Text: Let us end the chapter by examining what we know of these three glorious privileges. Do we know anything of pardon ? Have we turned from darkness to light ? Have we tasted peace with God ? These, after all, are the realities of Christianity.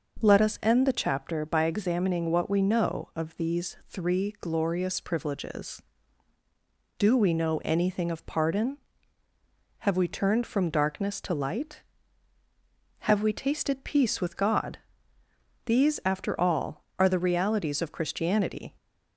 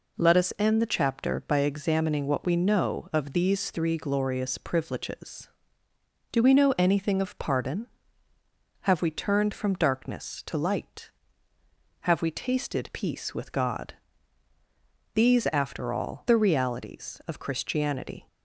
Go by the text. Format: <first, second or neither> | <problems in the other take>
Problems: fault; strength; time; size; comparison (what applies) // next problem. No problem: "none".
first | skips "are"; at 16.2 s